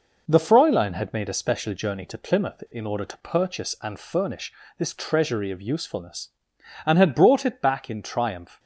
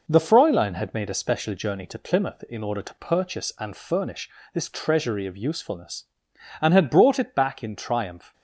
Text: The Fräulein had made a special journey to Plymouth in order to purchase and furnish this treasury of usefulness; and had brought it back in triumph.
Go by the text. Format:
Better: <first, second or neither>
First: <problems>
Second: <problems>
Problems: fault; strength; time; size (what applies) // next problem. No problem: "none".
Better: neither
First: pauses between "furnish" and "this"; slight; at 4.5 s; 0.28 s long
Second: pauses between "furnish" and "this"; slight; at 4.2 s; 0.26 s long